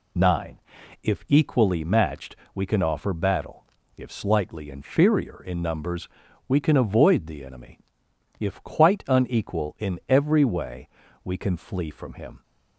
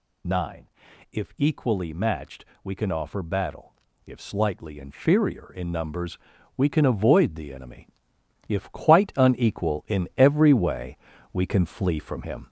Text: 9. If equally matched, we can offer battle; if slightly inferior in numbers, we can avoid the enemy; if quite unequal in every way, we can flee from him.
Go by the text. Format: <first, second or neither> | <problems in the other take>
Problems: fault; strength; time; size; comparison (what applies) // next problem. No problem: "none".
first | gets louder; noticeable; throughout; 4.5 dB